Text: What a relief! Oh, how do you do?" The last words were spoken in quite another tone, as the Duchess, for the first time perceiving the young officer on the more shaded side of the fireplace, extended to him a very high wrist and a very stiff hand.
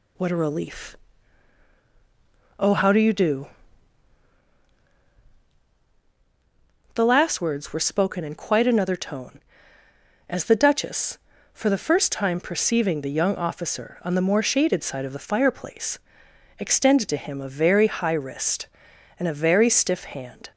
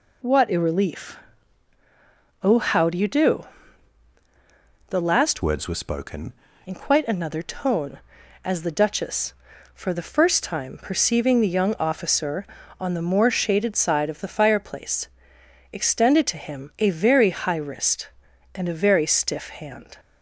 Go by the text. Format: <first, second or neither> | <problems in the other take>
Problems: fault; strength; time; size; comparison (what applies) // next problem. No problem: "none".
first | changes voice from "words" to "spoken"; from 5.4 to 6.3 s; 0.9 s long